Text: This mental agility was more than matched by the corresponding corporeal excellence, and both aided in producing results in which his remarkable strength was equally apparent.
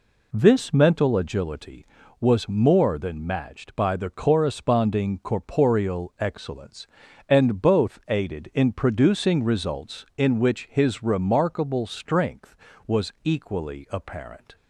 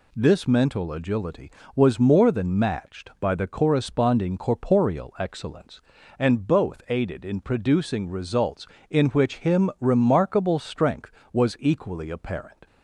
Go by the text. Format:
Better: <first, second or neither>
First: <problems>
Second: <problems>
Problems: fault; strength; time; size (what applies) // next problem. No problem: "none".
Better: first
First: none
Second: says "him" for "his"; at 9.3 s